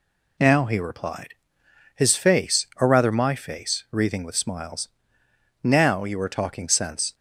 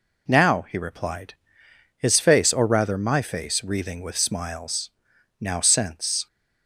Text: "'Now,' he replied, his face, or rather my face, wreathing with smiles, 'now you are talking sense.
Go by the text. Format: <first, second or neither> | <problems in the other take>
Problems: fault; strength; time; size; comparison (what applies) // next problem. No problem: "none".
first | skips "you are talking"; at 5.6 s